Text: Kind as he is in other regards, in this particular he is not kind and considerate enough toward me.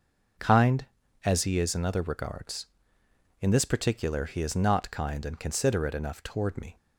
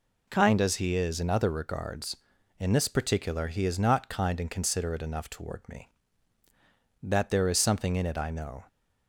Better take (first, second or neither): first